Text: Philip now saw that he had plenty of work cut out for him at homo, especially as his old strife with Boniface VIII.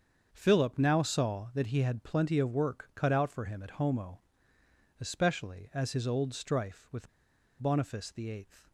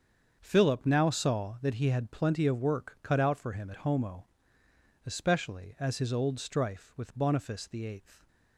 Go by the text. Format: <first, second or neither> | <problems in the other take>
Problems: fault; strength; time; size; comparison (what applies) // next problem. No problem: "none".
second | starts louder than the rest; strong; until 1.3 s; 7 dB; strong in the second // pauses between "with" and "Boniface"; noticeable; at 7.0 s; 0.51 s long